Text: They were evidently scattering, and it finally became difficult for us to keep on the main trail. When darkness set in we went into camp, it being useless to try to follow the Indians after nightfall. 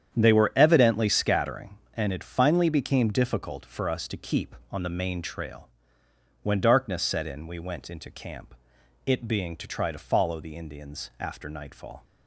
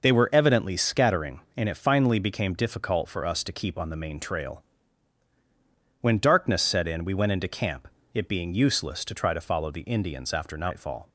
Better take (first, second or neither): second